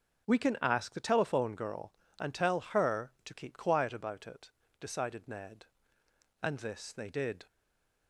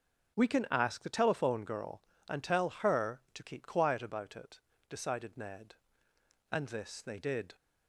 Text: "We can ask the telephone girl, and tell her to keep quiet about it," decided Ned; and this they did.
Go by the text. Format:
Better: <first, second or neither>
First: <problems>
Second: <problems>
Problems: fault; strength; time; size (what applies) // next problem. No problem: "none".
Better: second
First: starts louder than the rest; until 1.3 s; 6.5 dB // stays silent after the last word; slight; from 7.4 s on; 0.6 s long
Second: starts louder than the rest; until 1.4 s; 6.5 dB